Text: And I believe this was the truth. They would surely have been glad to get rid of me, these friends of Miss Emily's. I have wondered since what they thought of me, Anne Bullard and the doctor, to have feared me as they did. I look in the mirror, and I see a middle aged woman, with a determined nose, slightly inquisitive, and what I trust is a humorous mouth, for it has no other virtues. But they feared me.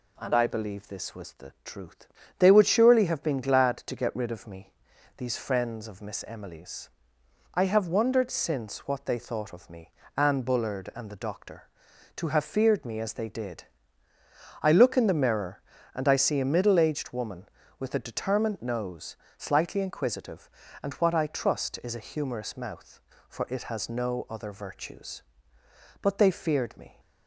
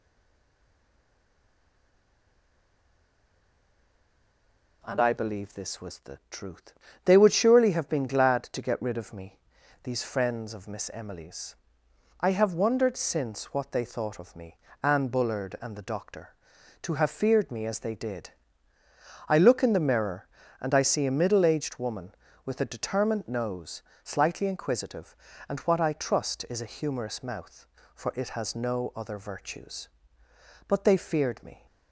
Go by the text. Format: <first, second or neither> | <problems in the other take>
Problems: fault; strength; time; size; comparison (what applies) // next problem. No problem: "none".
first | stays silent before the first word; strong; until 4.8 s; 4.8 s long